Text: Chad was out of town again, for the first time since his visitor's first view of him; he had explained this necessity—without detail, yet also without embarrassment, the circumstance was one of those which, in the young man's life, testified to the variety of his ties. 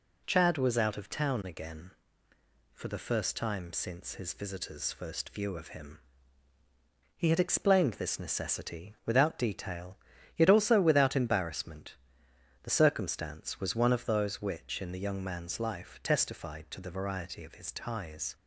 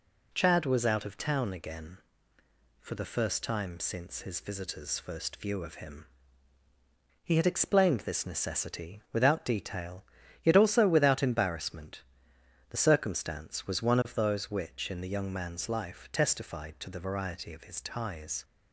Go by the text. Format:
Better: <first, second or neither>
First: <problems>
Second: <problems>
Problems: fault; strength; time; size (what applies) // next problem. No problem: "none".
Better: neither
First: none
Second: none